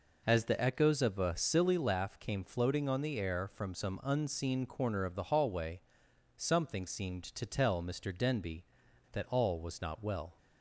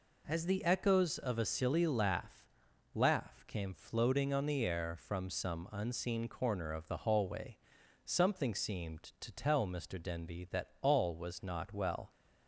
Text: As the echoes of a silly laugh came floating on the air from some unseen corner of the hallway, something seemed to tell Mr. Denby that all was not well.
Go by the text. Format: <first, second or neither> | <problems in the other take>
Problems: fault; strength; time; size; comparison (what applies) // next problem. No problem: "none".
first | says "laugh" twice; at 2.9 s